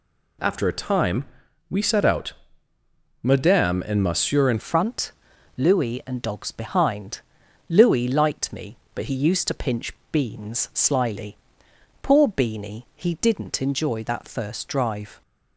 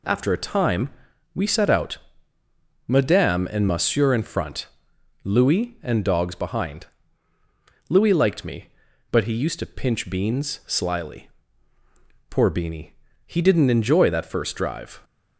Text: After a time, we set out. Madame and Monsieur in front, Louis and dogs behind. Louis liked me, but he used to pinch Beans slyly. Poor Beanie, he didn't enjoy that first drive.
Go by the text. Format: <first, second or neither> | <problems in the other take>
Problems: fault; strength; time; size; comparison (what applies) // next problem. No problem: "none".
second | changes voice at "front"; from 4.5 s on; 10.7 s long // pauses between "pinch" and "Beans"; slight; at 9.9 s; 0.18 s long